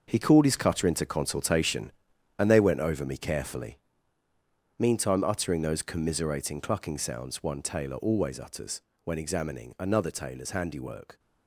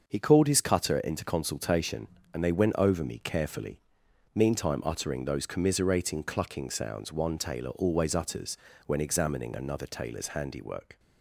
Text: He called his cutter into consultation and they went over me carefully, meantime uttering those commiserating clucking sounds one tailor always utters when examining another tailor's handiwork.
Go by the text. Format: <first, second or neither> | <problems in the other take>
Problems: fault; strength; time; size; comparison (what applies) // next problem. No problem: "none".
second | gets quieter; strong; throughout; 11 dB // starts louder than the rest; until 1.0 s; 6.5 dB; also in the second // pauses between "utters" and "when"; slight; at 8.8 s; 0.22 s long; slight in the second